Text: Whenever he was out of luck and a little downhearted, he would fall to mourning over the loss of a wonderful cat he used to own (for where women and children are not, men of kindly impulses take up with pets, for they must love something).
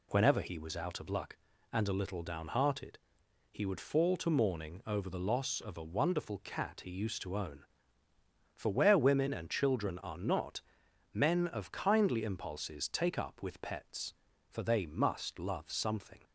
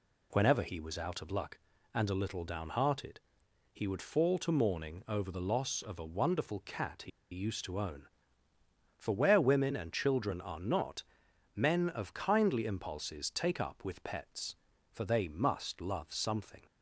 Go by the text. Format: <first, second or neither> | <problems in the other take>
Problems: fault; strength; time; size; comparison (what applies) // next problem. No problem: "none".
first | pauses between "he" and "used"; slight; at 7.1 s; 0.22 s long